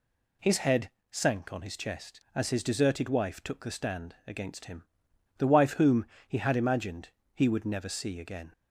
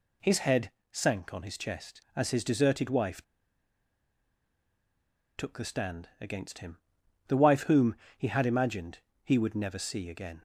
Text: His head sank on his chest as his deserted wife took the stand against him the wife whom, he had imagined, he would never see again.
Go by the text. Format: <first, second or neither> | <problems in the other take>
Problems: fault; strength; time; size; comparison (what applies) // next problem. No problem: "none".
first | pauses between "head" and "sank"; slight; at 0.7 s; 0.20 s long; slight in the first // pauses between "wife" and "took"; strong; at 3.2 s; 2.1 s long // pauses between "him" and "the"; noticeable; at 6.7 s; 0.50 s long; noticeable in the first